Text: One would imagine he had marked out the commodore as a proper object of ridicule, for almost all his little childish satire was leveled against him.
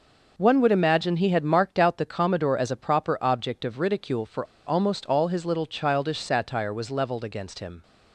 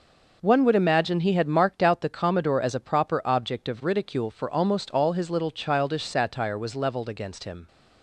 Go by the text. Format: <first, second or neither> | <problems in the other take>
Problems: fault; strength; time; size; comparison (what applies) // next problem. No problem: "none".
second | pauses between "for" and "almost"; slight; at 4.4 s; 0.22 s long